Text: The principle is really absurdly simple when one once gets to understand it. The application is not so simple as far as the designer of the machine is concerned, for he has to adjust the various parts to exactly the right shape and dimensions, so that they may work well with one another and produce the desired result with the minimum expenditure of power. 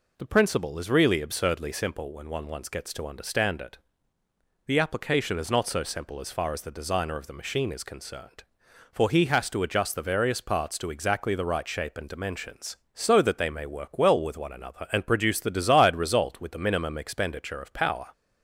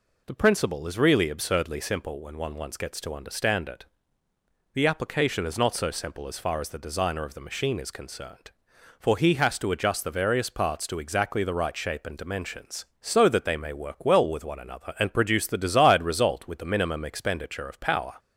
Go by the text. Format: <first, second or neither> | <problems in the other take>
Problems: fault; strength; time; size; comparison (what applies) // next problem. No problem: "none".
neither | none